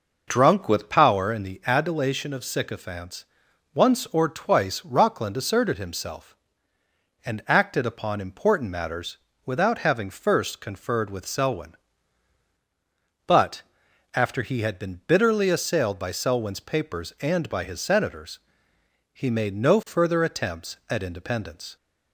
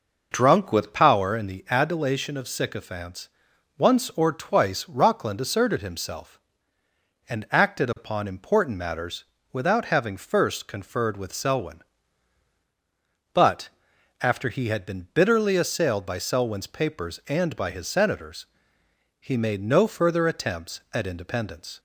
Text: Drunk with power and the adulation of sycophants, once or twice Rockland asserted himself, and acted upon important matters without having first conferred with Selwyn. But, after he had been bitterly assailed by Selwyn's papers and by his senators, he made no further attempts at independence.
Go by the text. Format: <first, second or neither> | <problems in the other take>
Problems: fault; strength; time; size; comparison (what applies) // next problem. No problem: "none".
neither | pauses between "matters" and "without"; slight; the same in both